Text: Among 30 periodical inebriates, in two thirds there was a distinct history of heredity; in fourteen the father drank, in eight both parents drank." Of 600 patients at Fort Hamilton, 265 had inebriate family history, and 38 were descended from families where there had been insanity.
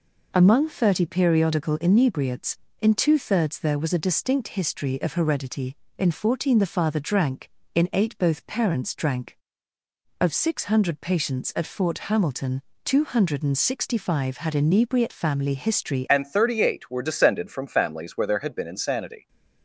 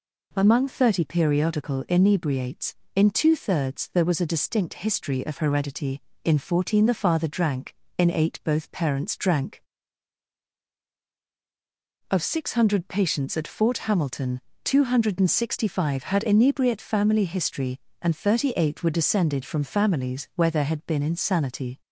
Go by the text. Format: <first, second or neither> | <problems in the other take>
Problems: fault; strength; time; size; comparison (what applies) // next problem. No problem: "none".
second | changes voice at "and"; from 16.0 s on; 3.2 s long